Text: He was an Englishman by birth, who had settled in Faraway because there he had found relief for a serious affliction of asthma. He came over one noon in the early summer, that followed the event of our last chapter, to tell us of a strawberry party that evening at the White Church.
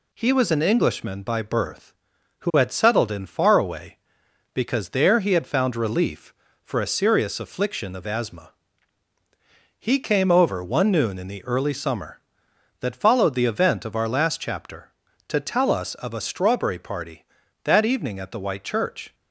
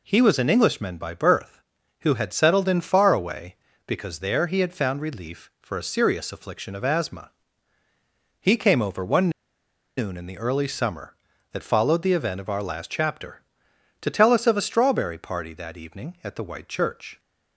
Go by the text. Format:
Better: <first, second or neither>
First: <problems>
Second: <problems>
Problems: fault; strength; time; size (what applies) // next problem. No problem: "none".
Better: first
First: none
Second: pauses between "one" and "noon"; noticeable; at 9.2 s; 0.67 s long